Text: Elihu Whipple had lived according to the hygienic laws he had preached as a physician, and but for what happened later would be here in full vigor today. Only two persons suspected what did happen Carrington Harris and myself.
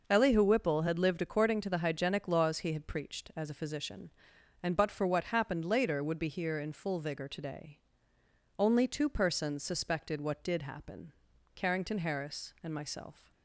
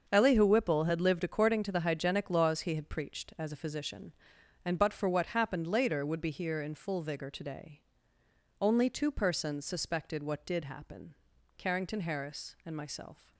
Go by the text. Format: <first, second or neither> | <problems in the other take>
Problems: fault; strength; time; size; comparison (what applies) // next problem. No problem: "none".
first | gets quieter; strong; throughout; 11.5 dB // pauses between "happen" and "Carrington"; at 11.1 s; 0.44 s long; also in the first